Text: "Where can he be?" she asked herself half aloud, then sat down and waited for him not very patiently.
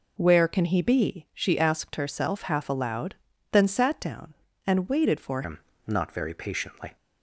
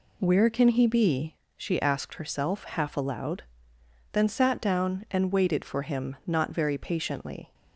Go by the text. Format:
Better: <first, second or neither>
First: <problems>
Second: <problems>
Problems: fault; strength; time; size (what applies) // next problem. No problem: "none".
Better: second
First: changes voice at "him"; from 5.4 s on; 1.5 s long // pauses between "him" and "not"; slight; at 5.5 s; 0.28 s long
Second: none